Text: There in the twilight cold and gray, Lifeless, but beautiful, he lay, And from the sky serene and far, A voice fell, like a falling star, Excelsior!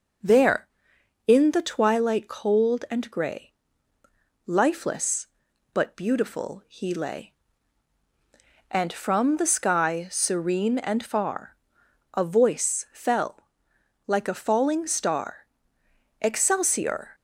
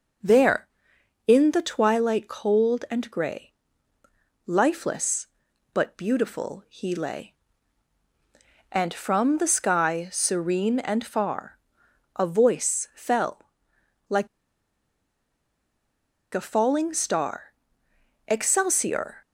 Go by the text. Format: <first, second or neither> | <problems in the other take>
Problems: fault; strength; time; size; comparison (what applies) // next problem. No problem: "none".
first | pauses between "like" and "a"; strong; at 14.2 s; 2.0 s long